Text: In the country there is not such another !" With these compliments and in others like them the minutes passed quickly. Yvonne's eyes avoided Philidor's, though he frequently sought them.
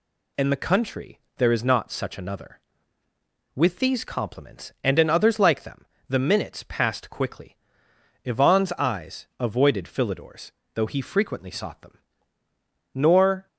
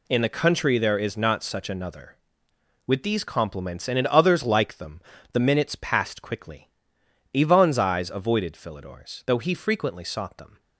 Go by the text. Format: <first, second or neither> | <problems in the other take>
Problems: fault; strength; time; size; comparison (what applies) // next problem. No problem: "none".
second | pauses between "country" and "there"; slight; at 1.1 s; 0.18 s long // pauses between "them" and "the"; slight; at 5.8 s; 0.24 s long; slight in the second // goes on to say "Nor"; from 12.9 s on; 0.54 s long